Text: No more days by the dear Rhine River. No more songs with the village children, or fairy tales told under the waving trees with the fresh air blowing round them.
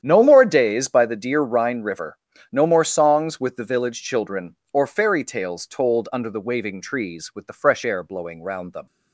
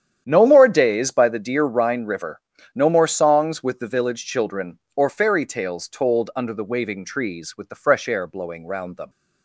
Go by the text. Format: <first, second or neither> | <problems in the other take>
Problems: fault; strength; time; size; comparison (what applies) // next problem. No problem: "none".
neither | starts louder than the rest; strong; the same in both